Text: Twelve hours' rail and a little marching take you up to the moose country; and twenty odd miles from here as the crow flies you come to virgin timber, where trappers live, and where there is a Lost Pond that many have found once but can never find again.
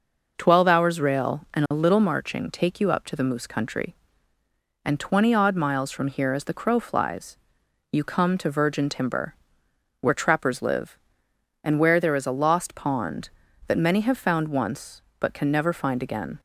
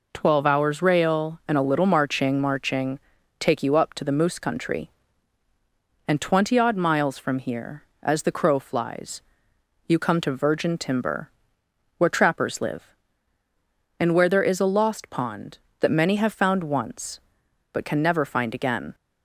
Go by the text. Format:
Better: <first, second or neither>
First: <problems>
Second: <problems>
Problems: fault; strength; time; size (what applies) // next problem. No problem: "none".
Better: first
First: pauses between "flies" and "you"; noticeable; at 7.3 s; 0.56 s long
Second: says "marching" twice; at 2.3 s // pauses between "flies" and "you"; noticeable; at 9.2 s; 0.64 s long